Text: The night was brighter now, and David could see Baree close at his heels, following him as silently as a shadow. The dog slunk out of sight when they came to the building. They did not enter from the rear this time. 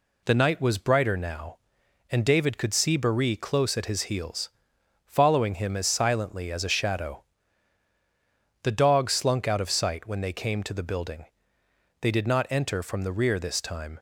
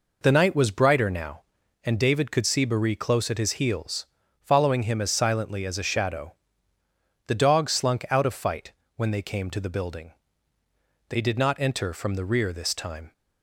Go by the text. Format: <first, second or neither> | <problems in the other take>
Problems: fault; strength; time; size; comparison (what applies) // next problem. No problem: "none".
first | says "fight" for "sight"; at 8.3 s